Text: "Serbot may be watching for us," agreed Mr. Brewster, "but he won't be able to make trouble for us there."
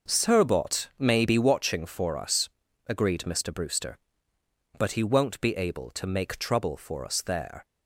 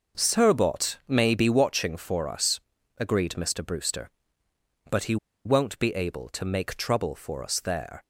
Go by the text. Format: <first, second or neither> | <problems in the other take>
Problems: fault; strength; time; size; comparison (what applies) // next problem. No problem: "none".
first | pauses between "he" and "won't"; slight; at 5.1 s; 0.29 s long